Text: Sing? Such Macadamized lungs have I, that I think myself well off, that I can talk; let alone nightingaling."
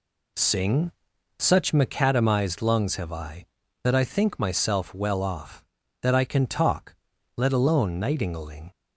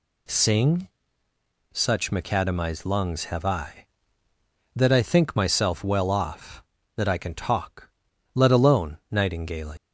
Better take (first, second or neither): first